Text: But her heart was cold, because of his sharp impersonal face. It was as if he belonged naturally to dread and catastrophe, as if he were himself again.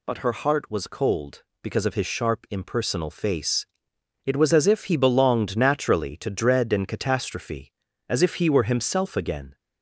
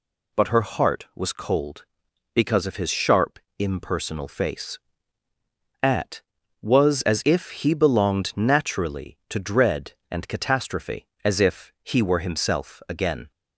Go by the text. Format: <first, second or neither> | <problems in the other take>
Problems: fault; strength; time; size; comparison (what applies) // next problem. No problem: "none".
first | pauses between "sharp" and "impersonal"; slight; at 3.3 s; 0.20 s long // says "At" for "It"; at 5.8 s